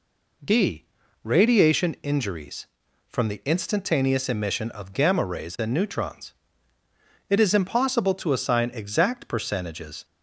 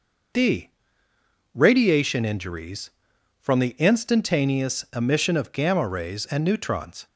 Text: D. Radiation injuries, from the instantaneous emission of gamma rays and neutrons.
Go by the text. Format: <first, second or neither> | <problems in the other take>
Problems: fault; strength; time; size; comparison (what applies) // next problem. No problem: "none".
second | goes on to say "It is impossible to assign exact percentages"; strong; from 7.2 s on; 2.7 s long